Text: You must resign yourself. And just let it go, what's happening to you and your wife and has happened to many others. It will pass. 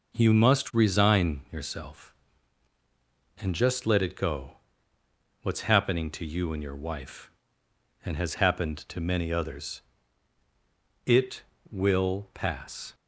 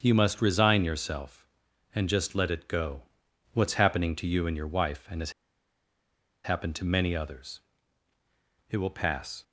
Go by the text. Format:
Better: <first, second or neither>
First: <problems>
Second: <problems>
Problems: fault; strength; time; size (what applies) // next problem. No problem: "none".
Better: first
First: none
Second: starts louder than the rest; until 1.0 s; 7 dB // pauses between "has" and "happened"; at 5.3 s; 1.1 s long